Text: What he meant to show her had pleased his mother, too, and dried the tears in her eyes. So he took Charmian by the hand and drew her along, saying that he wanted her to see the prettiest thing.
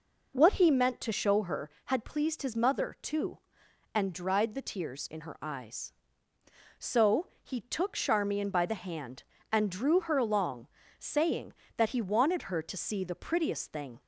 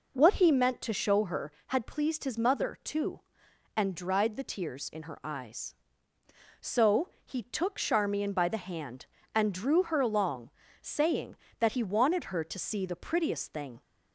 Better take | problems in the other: neither | pauses between "So" and "he"; slight; the same in both

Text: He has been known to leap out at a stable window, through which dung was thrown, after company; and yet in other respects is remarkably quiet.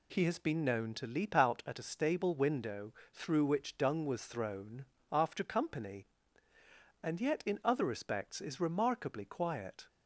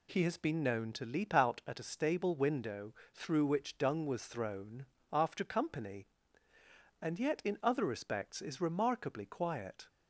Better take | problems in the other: neither | none

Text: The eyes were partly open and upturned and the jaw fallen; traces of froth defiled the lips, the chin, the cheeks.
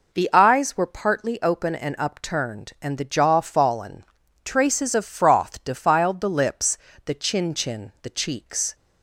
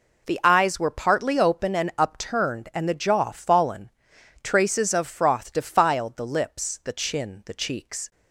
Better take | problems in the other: second | says "chin" twice; at 7.5 s

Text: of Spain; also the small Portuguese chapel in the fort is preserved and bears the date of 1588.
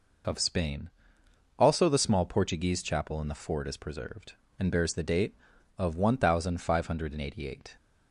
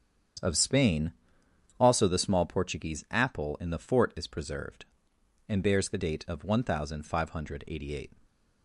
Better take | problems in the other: first | starts louder than the rest; strong; until 2.1 s; 8.5 dB // says "apple" for "chapel"; at 3.0 s // stays silent after the last word; slight; from 8.1 s on; 0.5 s long

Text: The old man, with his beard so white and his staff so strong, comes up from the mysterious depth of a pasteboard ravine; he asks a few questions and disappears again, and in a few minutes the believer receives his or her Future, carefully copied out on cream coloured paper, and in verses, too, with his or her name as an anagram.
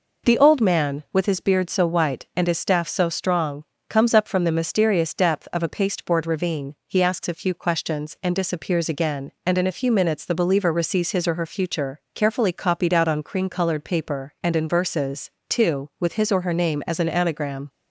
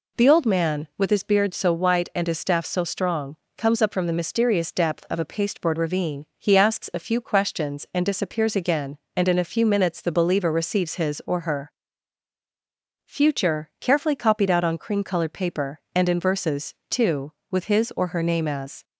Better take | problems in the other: first | pauses between "her" and "Future"; strong; at 11.7 s; 1.3 s long // stops before "an anagram"; at 18.8 s

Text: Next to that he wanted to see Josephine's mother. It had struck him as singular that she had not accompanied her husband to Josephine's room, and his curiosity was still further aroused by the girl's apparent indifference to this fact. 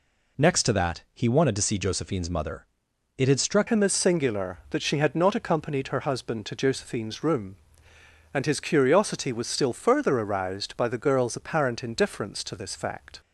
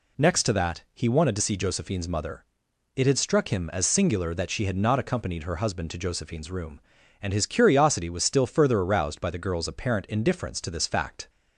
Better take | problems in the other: second | changes voice at "him"; from 3.6 s on; 9.5 s long

